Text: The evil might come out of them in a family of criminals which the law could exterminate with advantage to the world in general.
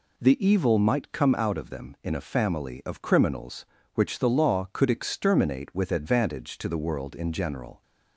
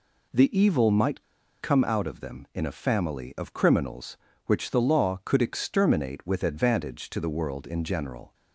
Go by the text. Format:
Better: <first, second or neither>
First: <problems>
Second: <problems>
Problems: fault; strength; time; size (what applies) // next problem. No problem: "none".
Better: first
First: none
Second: pauses between "might" and "come"; at 1.2 s; 0.37 s long